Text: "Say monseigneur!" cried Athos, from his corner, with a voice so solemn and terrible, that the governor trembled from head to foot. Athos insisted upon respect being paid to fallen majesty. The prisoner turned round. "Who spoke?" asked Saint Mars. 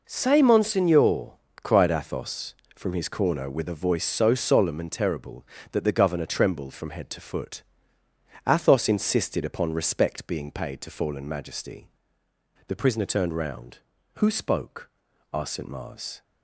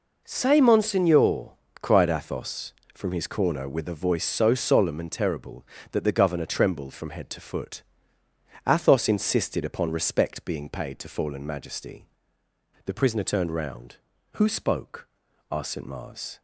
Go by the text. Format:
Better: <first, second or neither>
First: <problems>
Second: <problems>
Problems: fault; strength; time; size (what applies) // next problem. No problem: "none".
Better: neither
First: none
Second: none